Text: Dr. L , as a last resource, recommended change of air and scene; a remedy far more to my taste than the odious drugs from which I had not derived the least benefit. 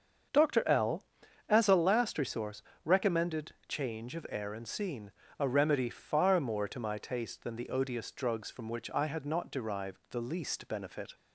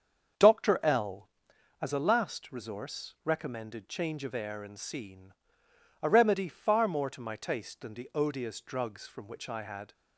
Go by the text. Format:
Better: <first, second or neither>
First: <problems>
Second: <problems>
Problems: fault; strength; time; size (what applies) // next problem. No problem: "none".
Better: first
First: starts louder than the rest; until 1.7 s; 7 dB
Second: starts louder than the rest; strong; until 1.8 s; 7 dB // stops before "not derived the least benefit"; at 9.9 s